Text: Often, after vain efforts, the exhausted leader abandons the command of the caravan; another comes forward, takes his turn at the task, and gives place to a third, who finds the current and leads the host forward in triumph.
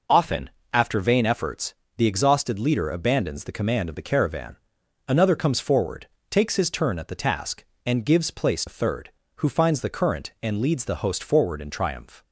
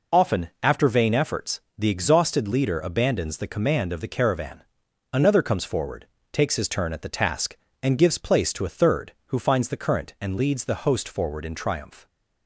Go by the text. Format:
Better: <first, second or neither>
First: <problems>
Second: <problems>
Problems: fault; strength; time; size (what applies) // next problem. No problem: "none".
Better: second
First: skips "to"; at 8.6 s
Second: none